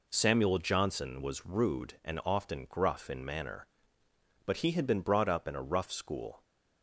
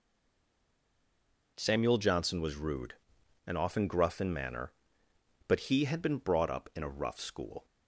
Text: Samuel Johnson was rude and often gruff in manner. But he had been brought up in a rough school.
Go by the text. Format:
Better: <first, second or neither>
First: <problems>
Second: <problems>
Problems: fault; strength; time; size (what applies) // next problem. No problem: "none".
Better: first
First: none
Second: stays silent before the first word; noticeable; until 1.5 s; 1.5 s long